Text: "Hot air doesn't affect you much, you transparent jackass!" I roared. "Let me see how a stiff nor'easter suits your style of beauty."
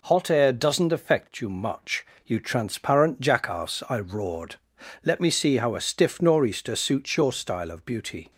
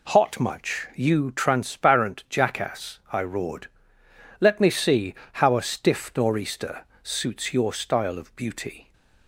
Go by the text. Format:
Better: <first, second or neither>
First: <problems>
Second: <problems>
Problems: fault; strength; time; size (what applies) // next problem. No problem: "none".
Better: first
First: none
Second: skips "air doesn't affect you"; at 0.3 s // pauses between "see" and "how"; slight; at 5.1 s; 0.28 s long // pauses between "nor'easter" and "suits"; slight; at 6.8 s; 0.18 s long